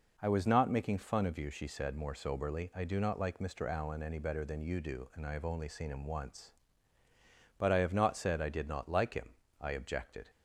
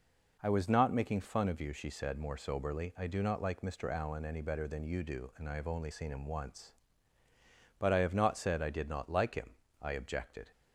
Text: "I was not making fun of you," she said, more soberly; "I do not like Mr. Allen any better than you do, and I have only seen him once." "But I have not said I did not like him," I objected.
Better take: neither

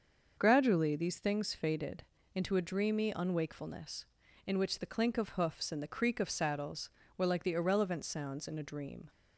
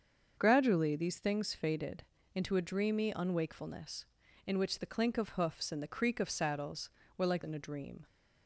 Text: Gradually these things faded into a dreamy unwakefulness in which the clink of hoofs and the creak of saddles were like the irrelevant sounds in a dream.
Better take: first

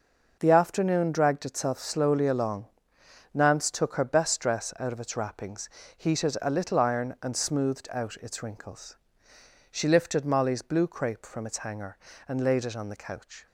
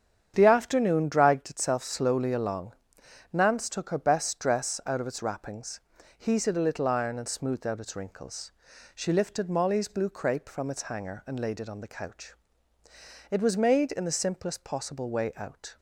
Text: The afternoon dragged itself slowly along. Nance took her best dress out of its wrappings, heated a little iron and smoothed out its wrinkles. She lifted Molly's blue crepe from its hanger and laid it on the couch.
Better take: first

